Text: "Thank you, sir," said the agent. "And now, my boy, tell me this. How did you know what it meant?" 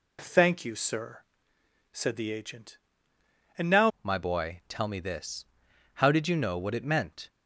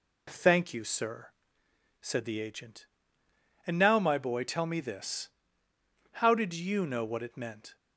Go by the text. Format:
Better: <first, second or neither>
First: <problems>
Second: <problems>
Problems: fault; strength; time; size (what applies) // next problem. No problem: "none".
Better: second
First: changes voice at "my"; from 4.0 s on; 3.2 s long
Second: none